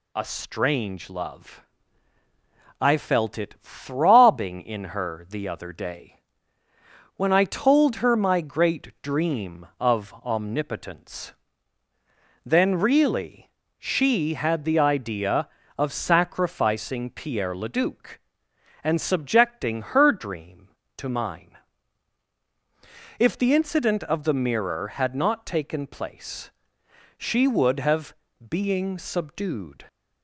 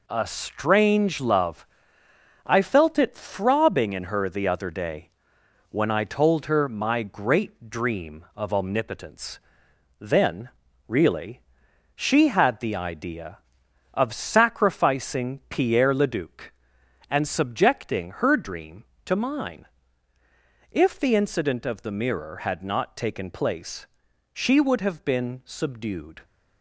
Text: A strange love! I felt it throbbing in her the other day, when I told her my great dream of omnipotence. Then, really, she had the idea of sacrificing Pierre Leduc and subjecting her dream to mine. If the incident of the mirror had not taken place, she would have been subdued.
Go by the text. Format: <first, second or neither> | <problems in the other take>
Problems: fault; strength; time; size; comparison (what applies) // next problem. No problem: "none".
second | says "being" for "been"; at 28.4 s